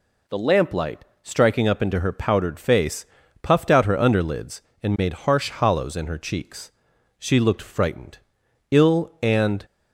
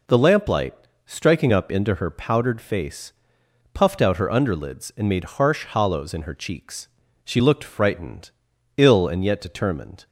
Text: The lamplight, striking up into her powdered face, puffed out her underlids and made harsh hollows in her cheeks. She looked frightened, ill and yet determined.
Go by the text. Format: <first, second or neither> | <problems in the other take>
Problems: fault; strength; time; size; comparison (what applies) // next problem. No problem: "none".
second | stops before "yet determined"; at 9.6 s